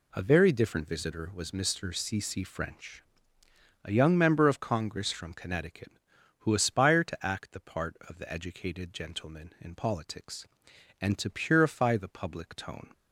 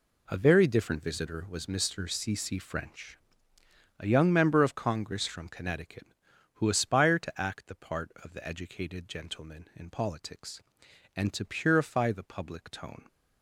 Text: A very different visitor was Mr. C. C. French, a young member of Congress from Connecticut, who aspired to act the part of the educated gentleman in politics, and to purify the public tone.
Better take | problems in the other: first | gets quieter; strong; throughout; 11.5 dB

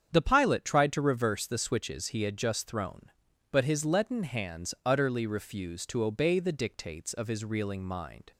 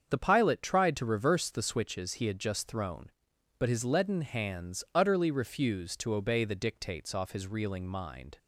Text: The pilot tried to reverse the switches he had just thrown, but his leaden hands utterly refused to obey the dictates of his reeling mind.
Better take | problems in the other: first | starts louder than the rest; until 1.1 s; 7 dB; strong in the first // says "off" for "of"; at 7.1 s

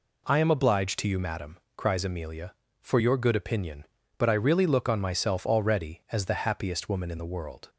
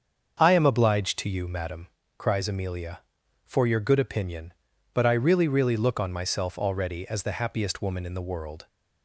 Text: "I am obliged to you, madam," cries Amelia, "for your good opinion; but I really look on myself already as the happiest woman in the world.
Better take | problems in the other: first | starts louder than the rest; until 1.4 s; 7 dB // says "really" twice; at 5.4 s

